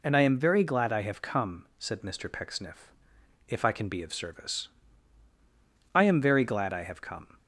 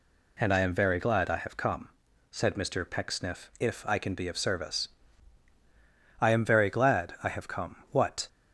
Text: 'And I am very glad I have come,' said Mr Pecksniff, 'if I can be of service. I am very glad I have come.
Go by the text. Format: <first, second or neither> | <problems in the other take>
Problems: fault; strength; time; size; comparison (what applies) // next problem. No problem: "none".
first | goes on to say "What"; slight; from 7.8 s on; 0.38 s long